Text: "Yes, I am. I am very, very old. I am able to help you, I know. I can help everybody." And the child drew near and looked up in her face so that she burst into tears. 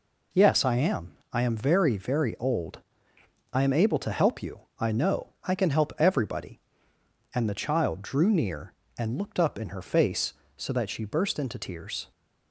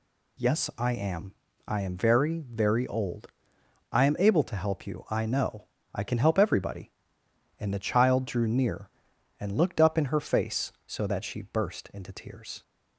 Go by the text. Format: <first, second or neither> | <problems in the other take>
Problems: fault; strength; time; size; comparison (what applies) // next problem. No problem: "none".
neither | none